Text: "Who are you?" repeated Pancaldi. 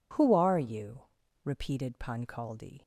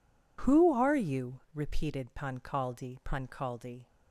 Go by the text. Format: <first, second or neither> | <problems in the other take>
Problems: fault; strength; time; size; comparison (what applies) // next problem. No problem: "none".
first | says "Pancaldi" twice; at 3.0 s